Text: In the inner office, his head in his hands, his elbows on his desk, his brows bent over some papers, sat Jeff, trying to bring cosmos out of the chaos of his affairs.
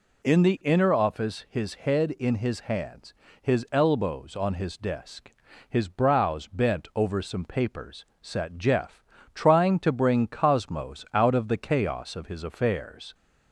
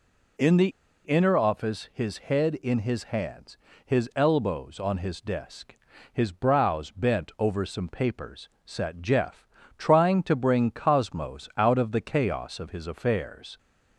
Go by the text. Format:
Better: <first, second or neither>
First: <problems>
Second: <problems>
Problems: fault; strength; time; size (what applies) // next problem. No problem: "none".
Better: first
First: none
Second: pauses between "the" and "inner"; slight; at 0.6 s; 0.35 s long